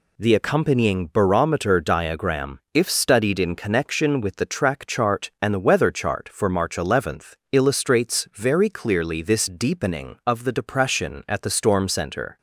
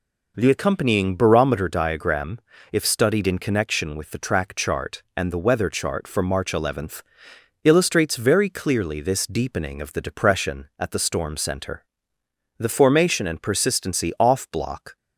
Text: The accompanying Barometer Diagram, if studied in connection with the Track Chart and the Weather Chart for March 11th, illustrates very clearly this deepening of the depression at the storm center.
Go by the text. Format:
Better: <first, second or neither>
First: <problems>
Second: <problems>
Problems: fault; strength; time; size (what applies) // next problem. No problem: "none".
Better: first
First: none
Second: goes on to say "The formation and persistency off Block"; strong; from 12.5 s on; 2.3 s long